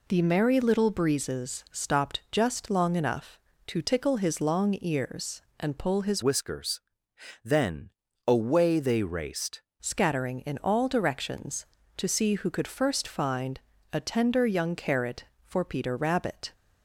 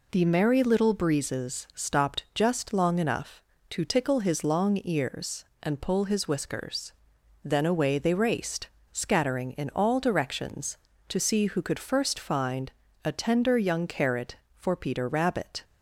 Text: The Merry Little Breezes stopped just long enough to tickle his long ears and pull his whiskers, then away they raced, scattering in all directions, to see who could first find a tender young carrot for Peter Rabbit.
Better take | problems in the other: second | changes voice from "whiskers" to "raced"; from 6.2 to 9.6 s; 3.4 s long // pauses between "then" and "away"; slight; at 7.9 s; 0.36 s long // pauses between "find" and "a"; slight; at 13.5 s; 0.32 s long; slight in the second

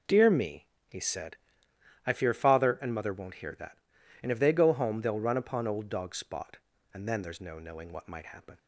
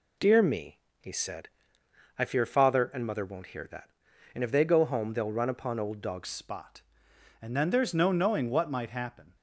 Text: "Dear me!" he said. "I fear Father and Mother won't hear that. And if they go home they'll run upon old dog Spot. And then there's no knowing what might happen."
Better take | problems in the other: first | changes voice at "Spot"; from 6.2 s on; 3.1 s long

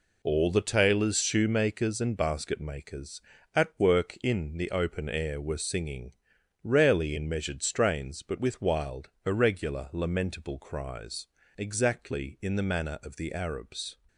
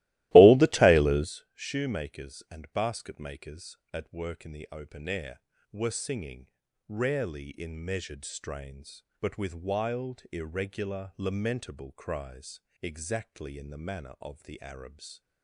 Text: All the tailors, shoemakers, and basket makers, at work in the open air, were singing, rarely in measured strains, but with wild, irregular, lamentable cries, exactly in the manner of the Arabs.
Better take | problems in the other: first | starts louder than the rest; strong; until 1.4 s; 18 dB

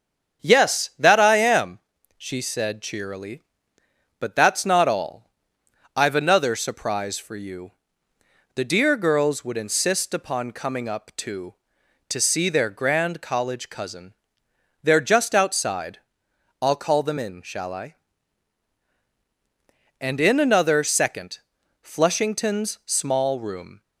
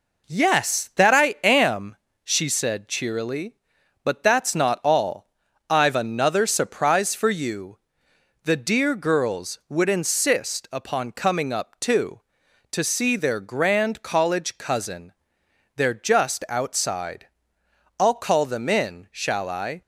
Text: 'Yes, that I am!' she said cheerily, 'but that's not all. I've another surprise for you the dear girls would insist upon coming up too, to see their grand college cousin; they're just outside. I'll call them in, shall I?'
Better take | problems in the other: second | starts louder than the rest; strong; until 1.5 s; 7.5 dB // pauses between "you" and "the"; noticeable; at 7.7 s; 0.84 s long; noticeable in the second // goes on to say "And in another second Flushington's small room"; strong; from 19.9 s on; 3.8 s long

